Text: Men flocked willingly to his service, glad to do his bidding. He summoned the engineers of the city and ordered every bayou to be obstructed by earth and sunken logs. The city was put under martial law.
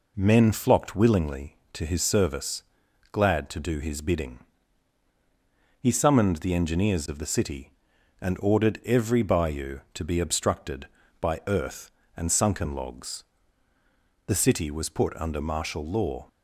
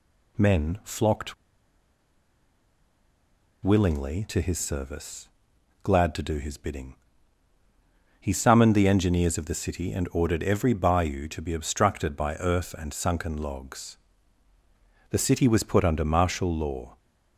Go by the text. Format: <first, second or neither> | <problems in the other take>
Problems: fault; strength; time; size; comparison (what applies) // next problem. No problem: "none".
first | pauses between "flocked" and "willingly"; strong; at 1.3 s; 2.3 s long